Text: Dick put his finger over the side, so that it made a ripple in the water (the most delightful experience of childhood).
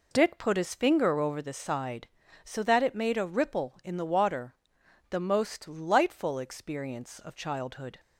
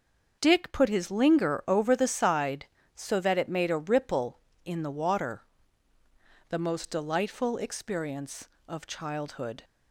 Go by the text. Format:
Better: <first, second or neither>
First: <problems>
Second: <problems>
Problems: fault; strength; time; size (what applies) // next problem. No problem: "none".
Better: first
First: none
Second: starts louder than the rest; until 1.4 s; 6.5 dB // says "linger" for "finger"; at 1.1 s